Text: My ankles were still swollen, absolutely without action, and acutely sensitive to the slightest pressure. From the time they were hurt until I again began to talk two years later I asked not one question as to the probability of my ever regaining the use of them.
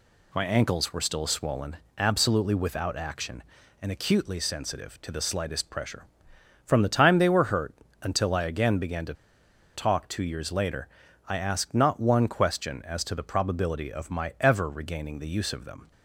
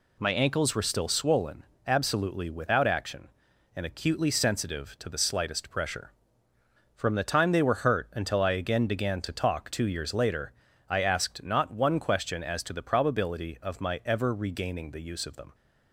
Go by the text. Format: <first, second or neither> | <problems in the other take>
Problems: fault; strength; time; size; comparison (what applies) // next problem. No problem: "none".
second | pauses between "hurt" and "until"; slight; at 7.7 s; 0.28 s long // pauses between "to" and "talk"; noticeable; at 9.1 s; 0.62 s long // pauses between "later" and "I"; at 10.8 s; 0.40 s long; slight in the second